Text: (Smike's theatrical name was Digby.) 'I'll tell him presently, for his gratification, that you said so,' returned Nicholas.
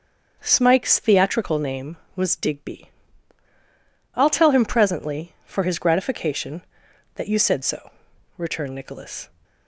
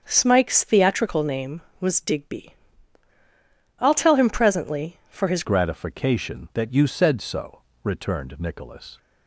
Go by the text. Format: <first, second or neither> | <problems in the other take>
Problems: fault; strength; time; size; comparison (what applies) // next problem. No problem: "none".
first | starts louder than the rest; until 1.0 s; 6.5 dB; also in the first // changes voice at "gratification"; from 5.4 s on; 3.5 s long